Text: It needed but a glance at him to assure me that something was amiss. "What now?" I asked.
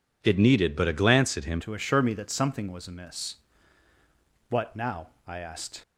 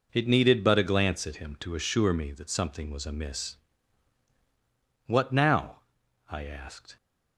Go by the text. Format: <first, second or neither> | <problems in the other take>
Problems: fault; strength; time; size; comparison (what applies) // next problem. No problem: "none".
second | changes voice at "to"; from 1.5 s on; 4.3 s long